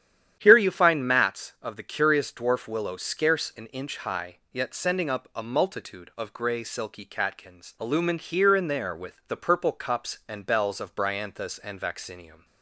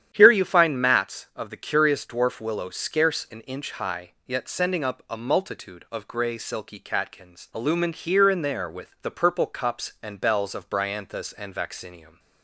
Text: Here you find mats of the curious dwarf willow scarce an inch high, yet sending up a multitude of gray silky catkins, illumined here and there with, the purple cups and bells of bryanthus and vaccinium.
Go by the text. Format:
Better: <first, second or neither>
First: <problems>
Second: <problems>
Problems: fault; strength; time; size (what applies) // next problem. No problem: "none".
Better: neither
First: starts louder than the rest; strong; until 1.4 s; 10 dB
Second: starts louder than the rest; strong; until 1.1 s; 10 dB